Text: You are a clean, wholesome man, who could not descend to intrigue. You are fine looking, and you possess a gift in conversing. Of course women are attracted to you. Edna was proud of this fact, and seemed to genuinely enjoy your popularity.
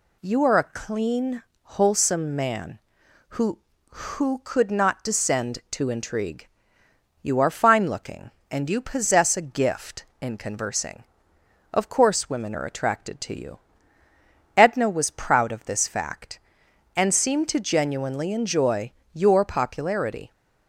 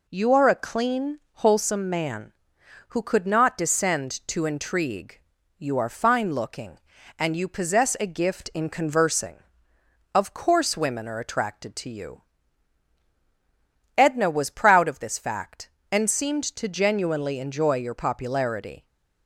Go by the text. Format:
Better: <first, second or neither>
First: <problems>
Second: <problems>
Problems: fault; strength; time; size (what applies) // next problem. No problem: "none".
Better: second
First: says "who" twice; at 3.9 s // pauses between "enjoy" and "your"; slight; at 18.9 s; 0.24 s long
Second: none